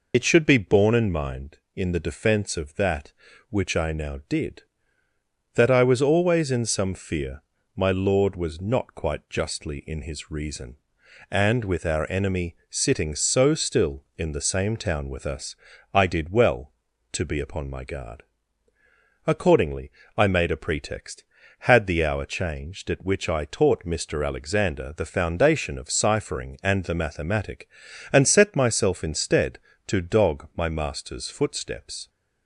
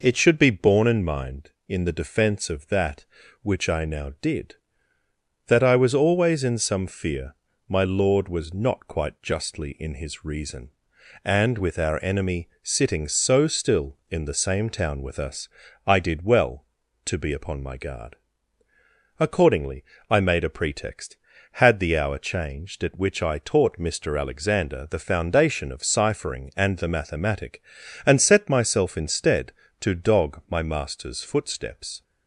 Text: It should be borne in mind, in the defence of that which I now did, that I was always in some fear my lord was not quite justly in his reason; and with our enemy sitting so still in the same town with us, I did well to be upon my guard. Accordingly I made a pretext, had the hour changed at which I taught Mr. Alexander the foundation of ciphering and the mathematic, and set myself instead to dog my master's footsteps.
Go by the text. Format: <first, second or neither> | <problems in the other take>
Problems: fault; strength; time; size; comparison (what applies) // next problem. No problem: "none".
second | loses the start of "It"; at 0.1 s; 70 ms // pauses between "fear" and "my"; slight; at 7.4 s; 0.34 s long; slight in the second // pauses between "Accordingly" and "I"; slight; at 19.9 s; 0.24 s long; slight in the second